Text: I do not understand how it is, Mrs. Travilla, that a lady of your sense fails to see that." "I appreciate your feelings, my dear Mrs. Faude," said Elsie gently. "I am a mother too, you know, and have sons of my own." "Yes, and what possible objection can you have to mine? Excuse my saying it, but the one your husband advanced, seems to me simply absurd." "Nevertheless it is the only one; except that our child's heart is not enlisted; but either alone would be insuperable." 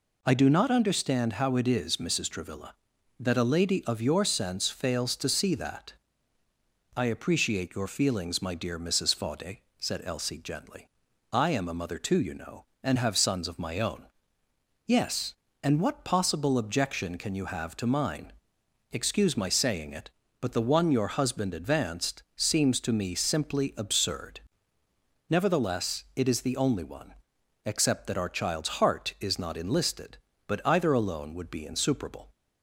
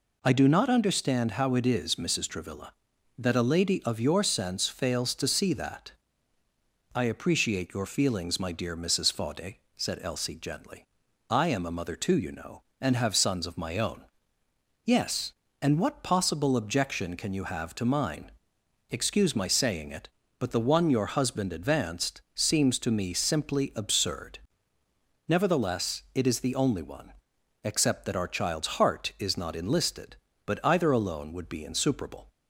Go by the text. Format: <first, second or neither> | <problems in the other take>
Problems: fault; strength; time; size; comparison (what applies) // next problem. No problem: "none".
neither | none